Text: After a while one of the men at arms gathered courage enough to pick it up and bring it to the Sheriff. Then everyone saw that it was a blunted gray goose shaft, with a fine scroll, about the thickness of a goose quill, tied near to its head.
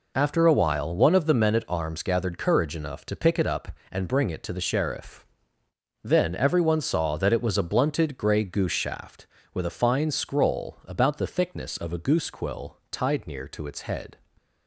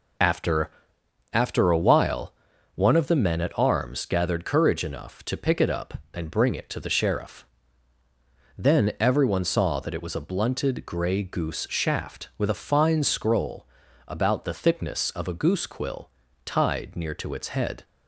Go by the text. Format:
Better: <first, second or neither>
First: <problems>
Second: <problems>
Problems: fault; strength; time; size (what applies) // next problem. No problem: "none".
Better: first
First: none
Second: says "After" twice; at 1.3 s // pauses between "while" and "one"; at 2.3 s; 0.40 s long